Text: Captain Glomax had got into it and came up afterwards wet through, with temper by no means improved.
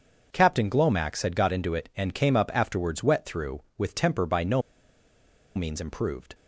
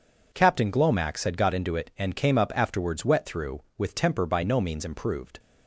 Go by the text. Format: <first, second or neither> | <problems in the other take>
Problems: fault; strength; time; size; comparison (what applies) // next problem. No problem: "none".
second | pauses between "no" and "means"; noticeable; at 4.6 s; 0.94 s long